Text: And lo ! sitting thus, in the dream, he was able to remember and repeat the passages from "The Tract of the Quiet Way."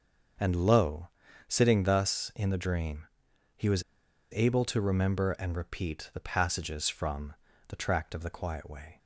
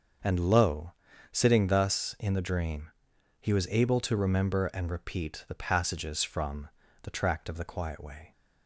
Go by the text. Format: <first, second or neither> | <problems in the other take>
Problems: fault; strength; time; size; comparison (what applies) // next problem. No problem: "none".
second | starts louder than the rest; until 1.8 s; 6.5 dB; also in the second // pauses between "was" and "able"; noticeable; at 3.8 s; 0.51 s long // pauses between "from" and "The"; slight; at 7.3 s; 0.34 s long; slight in the second